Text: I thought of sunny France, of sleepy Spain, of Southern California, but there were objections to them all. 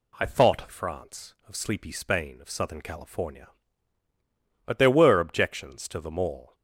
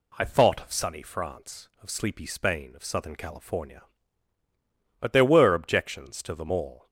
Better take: second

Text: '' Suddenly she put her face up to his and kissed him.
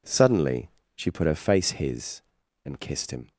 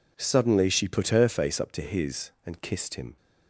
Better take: second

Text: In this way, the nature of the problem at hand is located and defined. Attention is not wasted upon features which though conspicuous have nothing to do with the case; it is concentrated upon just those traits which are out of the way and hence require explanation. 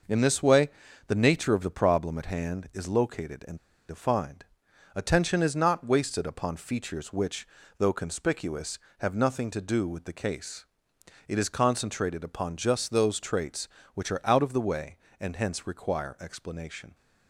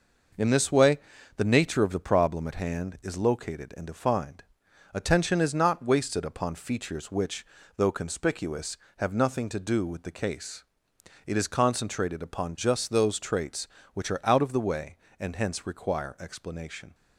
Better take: second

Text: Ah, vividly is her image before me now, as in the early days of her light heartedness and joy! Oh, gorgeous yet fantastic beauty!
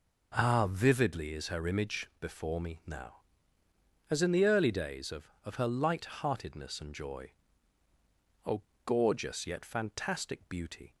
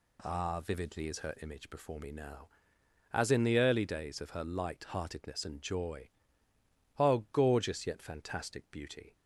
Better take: second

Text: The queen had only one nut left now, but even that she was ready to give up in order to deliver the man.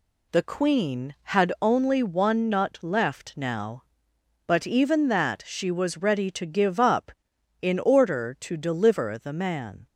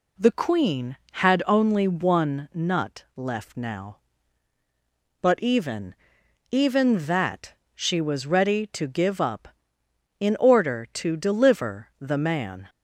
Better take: first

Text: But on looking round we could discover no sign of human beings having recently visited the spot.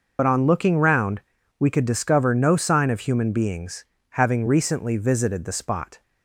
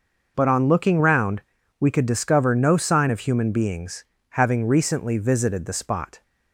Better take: second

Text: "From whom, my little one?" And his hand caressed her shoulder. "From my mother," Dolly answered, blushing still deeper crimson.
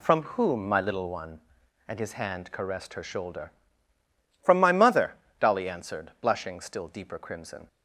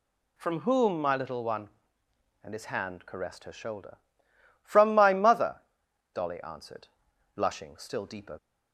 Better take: first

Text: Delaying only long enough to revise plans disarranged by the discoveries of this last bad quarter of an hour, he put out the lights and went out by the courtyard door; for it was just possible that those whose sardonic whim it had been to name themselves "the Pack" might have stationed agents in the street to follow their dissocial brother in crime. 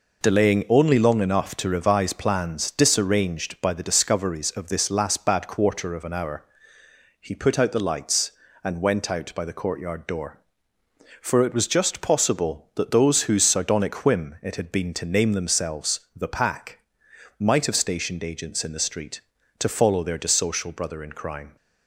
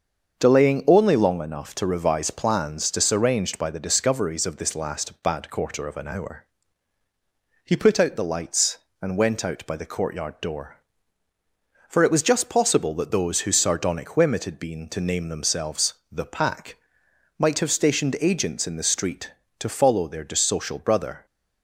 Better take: first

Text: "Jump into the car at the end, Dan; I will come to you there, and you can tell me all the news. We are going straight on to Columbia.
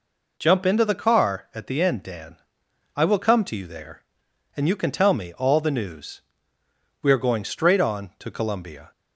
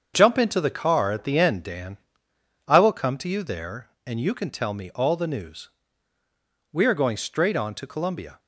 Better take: first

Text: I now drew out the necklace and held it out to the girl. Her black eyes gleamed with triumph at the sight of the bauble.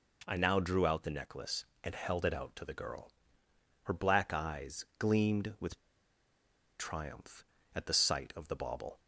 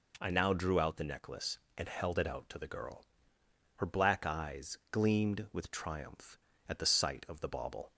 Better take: second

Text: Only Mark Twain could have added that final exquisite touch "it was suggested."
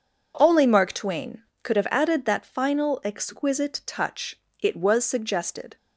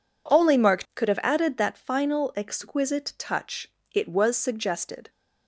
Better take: first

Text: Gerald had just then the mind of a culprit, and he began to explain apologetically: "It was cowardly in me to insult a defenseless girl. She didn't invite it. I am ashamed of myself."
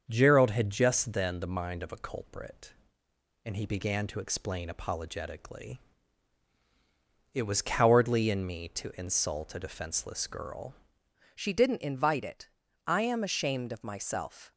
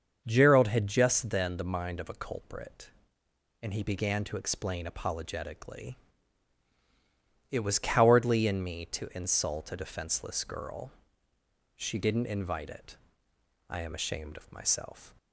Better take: second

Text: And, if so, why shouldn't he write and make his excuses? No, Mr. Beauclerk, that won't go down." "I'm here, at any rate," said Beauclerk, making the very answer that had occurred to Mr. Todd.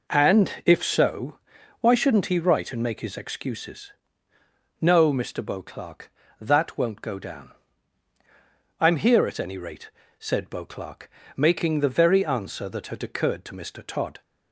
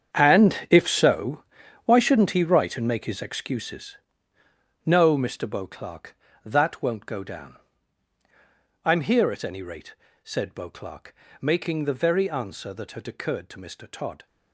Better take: first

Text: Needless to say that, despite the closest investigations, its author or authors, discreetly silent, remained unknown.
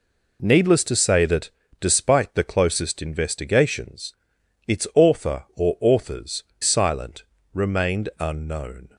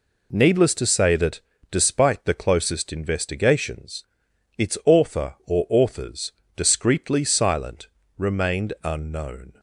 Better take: second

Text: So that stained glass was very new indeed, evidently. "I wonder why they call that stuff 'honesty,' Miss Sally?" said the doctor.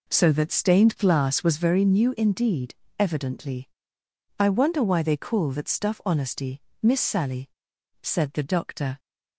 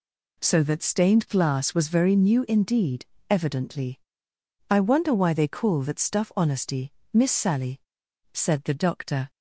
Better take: second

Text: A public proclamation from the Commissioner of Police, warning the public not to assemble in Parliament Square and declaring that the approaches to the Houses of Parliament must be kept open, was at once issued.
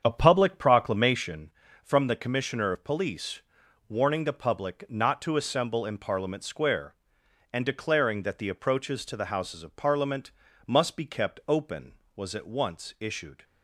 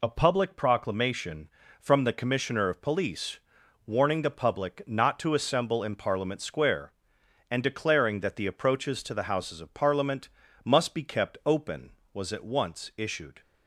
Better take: second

